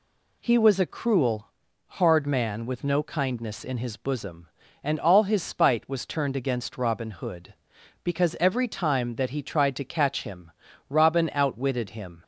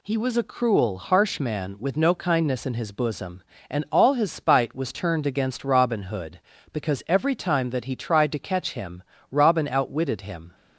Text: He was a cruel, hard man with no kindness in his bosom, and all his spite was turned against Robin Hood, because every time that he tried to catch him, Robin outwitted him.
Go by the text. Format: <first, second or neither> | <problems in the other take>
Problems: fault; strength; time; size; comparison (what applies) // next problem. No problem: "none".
first | says "harsh" for "hard"; at 0.9 s